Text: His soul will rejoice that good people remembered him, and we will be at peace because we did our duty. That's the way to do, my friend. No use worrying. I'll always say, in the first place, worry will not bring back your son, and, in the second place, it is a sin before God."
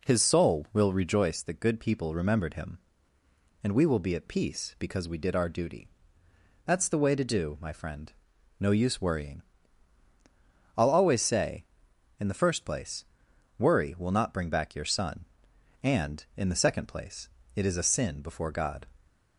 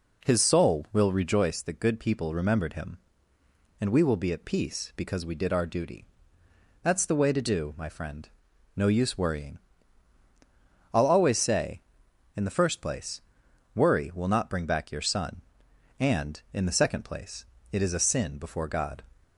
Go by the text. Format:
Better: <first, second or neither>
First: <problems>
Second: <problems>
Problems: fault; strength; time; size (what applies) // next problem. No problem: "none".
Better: neither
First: none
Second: none